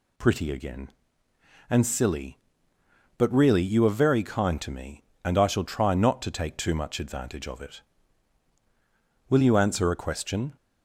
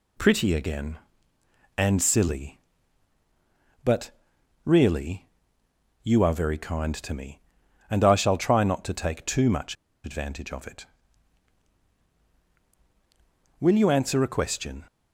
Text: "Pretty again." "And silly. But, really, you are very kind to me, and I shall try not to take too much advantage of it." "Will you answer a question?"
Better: first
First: none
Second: pauses between "much" and "advantage"; slight; at 9.7 s; 0.31 s long

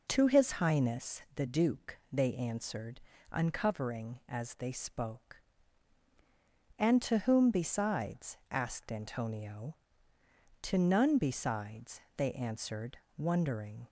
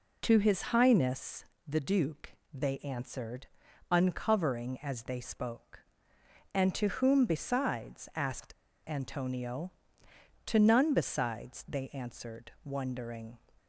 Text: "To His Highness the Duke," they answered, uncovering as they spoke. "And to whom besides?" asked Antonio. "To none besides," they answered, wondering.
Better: first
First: none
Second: pauses between "Highness" and "the"; slight; at 1.4 s; 0.20 s long // pauses between "asked" and "Antonio"; slight; at 8.5 s; 0.34 s long

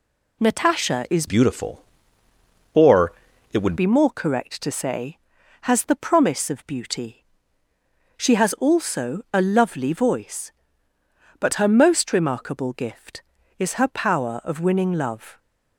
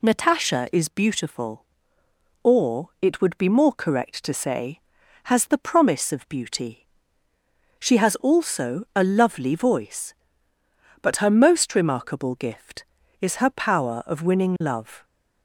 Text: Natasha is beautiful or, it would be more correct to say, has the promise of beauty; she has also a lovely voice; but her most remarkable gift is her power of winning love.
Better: second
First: changes voice from "beautiful" to "would"; from 1.2 to 3.7 s; 2.5 s long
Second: none

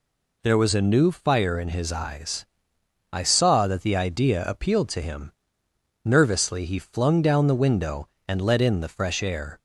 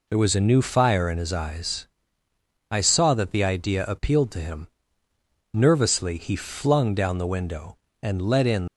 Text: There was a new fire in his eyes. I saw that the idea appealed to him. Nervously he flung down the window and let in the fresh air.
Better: first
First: none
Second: stops before "the fresh air"; at 8.6 s

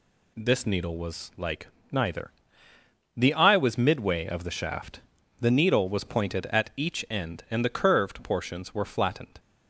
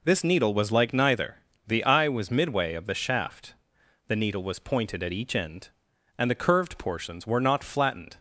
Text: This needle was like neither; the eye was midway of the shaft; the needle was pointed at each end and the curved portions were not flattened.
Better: second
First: pauses between "like" and "neither"; slight; at 1.6 s; 0.24 s long // skips "not"; at 8.8 s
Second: none

